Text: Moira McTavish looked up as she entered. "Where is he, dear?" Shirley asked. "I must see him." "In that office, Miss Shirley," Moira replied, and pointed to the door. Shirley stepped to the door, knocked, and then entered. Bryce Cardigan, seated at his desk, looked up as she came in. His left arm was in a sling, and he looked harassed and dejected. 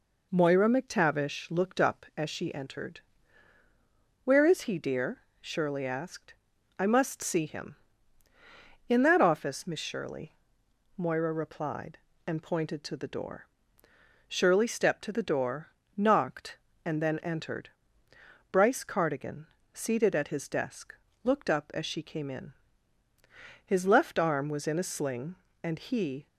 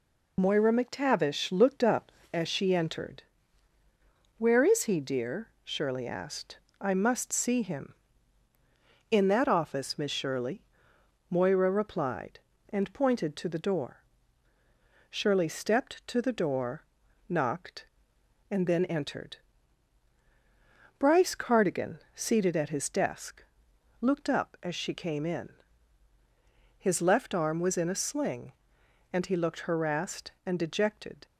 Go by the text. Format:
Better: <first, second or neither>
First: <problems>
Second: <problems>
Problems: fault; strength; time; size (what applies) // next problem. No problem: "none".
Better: second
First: stops before "looked harassed and dejected"; at 26.2 s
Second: none